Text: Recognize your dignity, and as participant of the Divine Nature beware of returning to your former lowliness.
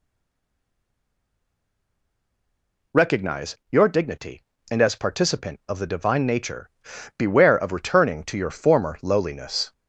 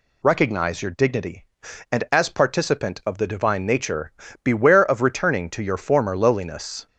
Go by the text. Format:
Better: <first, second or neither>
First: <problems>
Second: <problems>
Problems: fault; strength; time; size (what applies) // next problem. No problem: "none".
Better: second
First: stays silent before the first word; strong; until 2.9 s; 2.9 s long // pauses between "Nature" and "beware"; noticeable; at 6.6 s; 0.48 s long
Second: pauses between "Nature" and "beware"; slight; at 4.1 s; 0.32 s long